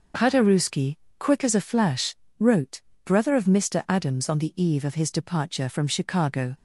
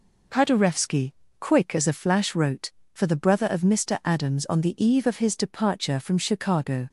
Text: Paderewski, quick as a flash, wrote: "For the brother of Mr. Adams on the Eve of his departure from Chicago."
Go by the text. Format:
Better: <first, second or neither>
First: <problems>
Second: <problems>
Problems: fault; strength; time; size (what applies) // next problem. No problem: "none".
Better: second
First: starts louder than the rest; noticeable; until 1.4 s; 6 dB // skips "For the"; at 2.9 s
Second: none